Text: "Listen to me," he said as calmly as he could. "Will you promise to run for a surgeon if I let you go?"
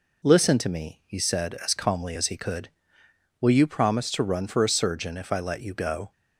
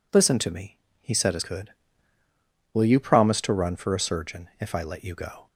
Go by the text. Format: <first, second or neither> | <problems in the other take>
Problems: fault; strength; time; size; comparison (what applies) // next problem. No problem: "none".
first | skips "calmly as he"; at 1.4 s